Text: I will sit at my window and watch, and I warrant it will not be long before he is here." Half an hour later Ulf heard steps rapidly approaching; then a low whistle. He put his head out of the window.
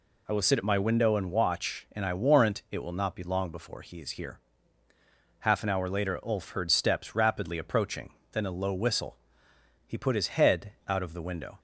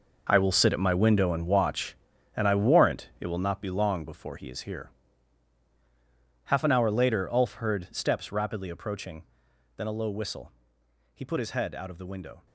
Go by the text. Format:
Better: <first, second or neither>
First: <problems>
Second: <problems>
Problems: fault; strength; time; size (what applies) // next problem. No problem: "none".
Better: first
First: none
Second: gets quieter; strong; throughout; 12 dB